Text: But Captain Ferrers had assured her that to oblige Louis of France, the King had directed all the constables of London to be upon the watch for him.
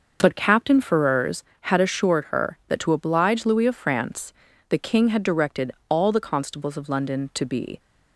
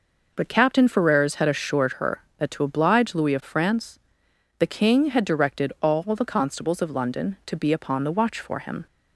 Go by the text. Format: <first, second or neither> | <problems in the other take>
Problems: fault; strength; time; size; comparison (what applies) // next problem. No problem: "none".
second | starts louder than the rest; noticeable; until 1.2 s; 6 dB // pauses between "directed" and "all"; slight; at 5.7 s; 0.16 s long // stops before "upon the watch for him"; at 7.7 s